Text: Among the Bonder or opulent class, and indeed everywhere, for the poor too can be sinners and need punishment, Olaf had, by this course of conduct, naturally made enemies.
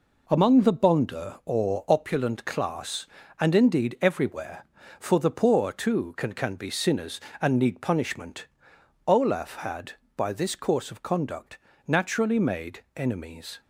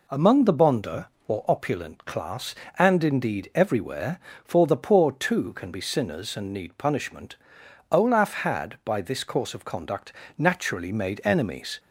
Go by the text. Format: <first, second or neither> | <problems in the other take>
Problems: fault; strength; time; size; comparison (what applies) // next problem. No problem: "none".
second | says "can" twice; at 6.3 s // pauses between "made" and "enemies"; slight; at 12.8 s; 0.16 s long